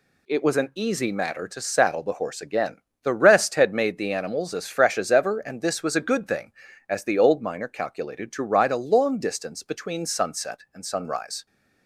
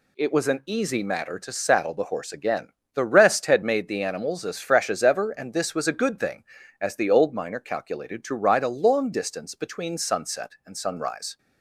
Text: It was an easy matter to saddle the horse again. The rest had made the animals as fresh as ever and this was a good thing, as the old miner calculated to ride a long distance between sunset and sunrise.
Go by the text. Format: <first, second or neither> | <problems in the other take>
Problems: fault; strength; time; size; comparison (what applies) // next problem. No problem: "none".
neither | none